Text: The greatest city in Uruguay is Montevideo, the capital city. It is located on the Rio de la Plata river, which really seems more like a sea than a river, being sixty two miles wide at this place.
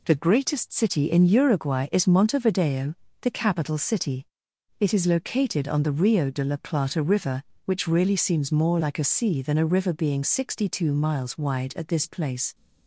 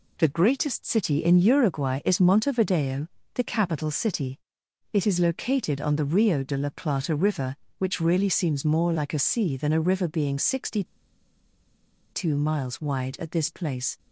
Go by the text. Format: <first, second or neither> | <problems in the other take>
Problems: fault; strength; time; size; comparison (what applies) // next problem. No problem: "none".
first | pauses between "sixty" and "two"; strong; at 10.8 s; 1.3 s long